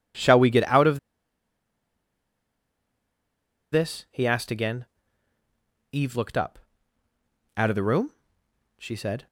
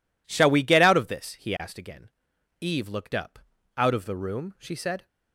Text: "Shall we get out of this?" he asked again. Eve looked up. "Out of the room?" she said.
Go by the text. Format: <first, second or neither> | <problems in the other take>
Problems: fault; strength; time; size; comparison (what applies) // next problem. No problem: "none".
second | pauses between "of" and "this"; strong; at 0.9 s; 2.7 s long